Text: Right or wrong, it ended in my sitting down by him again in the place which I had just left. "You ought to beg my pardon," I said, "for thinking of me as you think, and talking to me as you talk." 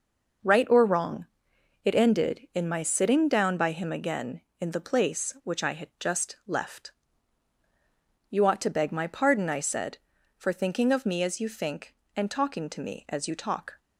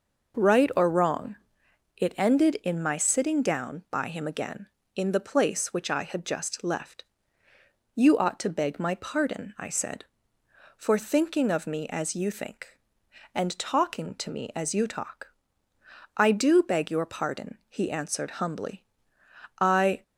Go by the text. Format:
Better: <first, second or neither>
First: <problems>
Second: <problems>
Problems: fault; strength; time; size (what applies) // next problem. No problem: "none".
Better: first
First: none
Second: goes on to say "I do beg your pardon he answered humbly I"; strong; from 16.1 s on; 3.8 s long